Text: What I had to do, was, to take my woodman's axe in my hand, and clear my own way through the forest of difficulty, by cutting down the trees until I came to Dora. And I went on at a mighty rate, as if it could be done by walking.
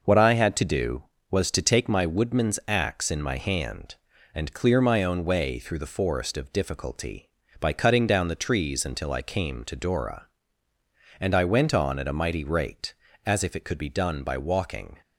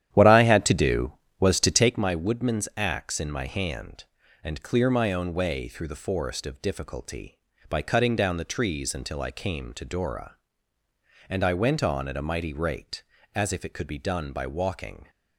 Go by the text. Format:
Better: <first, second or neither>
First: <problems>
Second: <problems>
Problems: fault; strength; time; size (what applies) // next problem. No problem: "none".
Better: first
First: none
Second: starts louder than the rest; strong; until 2.0 s; 11 dB